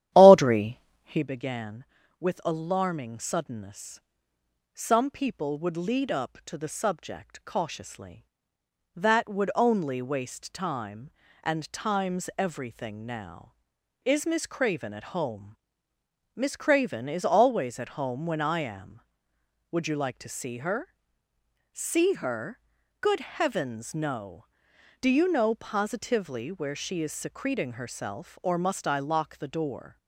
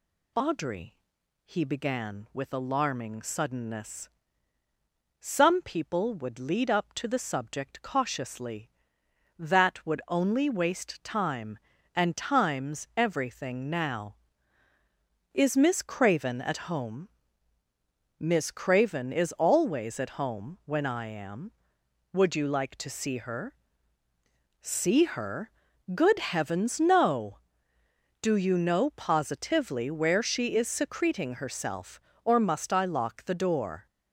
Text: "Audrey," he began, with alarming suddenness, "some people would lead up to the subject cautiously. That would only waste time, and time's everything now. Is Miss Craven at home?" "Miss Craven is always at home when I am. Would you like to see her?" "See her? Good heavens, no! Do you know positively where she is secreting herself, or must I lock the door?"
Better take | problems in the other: second | starts louder than the rest; strong; until 1.2 s; 11.5 dB

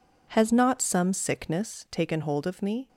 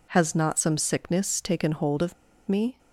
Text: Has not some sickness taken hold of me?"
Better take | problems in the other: first | pauses between "of" and "me"; slight; at 2.1 s; 0.33 s long

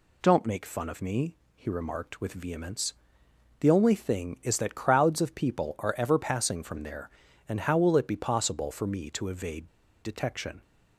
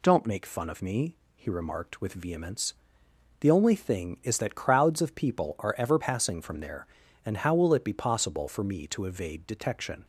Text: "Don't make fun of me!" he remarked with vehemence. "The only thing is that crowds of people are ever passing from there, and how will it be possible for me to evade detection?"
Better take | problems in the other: second | pauses between "evade" and "detection"; slight; at 9.6 s; 0.34 s long

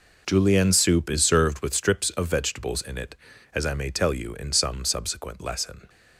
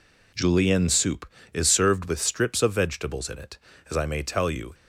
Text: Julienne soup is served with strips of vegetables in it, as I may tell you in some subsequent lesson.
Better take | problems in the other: first | stops before "in some subsequent lesson"; at 4.7 s

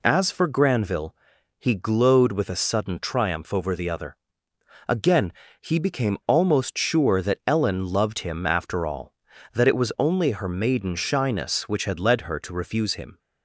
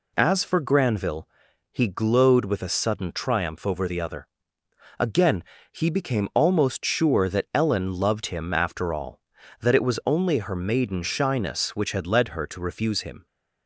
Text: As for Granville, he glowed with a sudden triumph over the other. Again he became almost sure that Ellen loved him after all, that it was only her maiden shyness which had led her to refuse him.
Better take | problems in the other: neither | pauses between "Again" and "he"; slight; the same in both

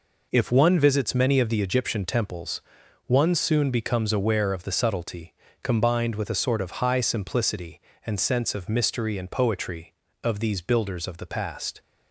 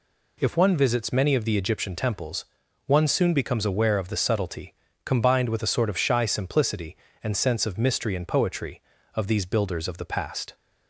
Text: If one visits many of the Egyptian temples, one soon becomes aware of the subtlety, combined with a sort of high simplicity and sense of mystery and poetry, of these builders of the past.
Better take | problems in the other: first | says "shy" for "high"; at 5.9 s

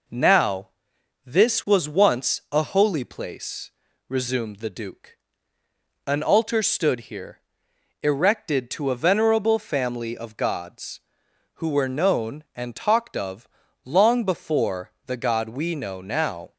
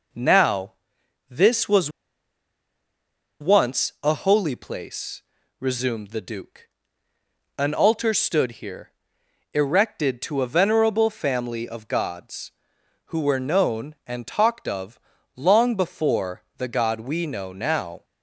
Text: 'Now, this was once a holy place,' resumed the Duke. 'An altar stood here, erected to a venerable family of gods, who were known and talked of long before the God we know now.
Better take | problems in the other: first | pauses between "was" and "once"; strong; at 1.8 s; 1.5 s long // pauses between "of" and "long"; at 14.9 s; 0.38 s long; also in the first

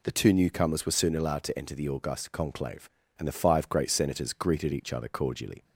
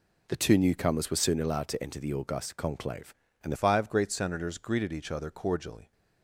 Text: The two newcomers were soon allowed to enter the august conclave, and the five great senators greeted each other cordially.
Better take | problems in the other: first | changes voice at "five"; from 3.5 s on; 2.4 s long

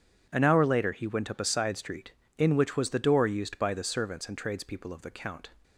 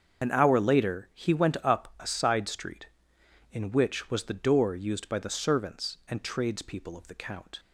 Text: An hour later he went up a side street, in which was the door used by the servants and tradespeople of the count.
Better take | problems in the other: first | loses the start of "An"; at 0.2 s; 70 ms // starts louder than the rest; until 1.2 s; 7 dB

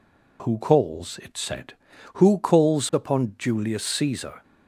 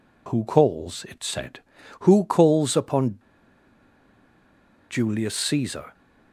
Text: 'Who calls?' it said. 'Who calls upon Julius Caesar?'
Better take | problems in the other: first | pauses between "upon" and "Julius"; strong; at 3.1 s; 1.7 s long

